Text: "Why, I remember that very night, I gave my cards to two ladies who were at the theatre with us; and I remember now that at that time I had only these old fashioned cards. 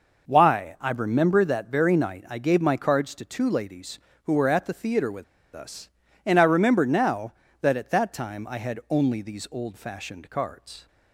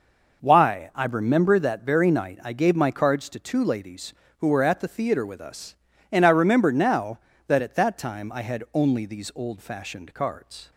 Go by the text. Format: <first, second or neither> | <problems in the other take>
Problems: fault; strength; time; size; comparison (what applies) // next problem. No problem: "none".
second | pauses between "with" and "us"; slight; at 5.2 s; 0.28 s long